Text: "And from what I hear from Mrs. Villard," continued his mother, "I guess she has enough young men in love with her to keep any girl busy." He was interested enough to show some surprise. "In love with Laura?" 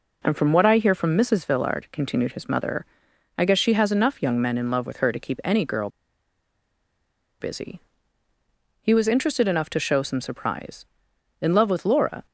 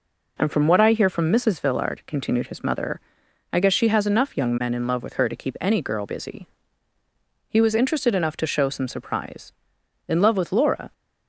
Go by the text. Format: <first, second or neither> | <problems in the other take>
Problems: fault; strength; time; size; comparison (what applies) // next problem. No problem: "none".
second | pauses between "girl" and "busy"; strong; at 5.8 s; 1.5 s long